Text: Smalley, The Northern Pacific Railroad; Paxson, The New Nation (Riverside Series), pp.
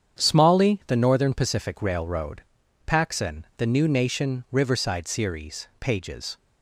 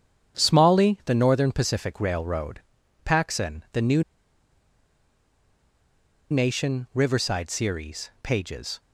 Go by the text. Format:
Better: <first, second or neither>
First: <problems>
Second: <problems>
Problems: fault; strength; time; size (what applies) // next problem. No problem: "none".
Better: first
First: starts louder than the rest; strong; until 1.2 s; 8.5 dB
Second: starts louder than the rest; strong; until 1.4 s; 8.5 dB // pauses between "New" and "Nation"; strong; at 4.0 s; 2.2 s long